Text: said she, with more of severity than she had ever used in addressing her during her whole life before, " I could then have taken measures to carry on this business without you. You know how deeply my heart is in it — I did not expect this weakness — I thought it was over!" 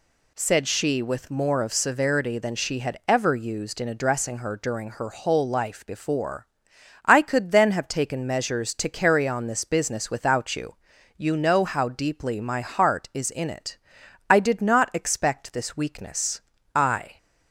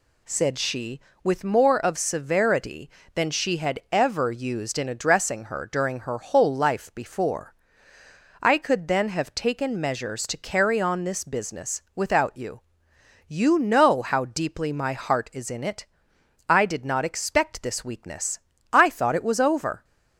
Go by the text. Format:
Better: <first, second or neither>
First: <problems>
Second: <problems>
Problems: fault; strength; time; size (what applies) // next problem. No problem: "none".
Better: second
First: stops before "thought it was over"; at 17.1 s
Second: none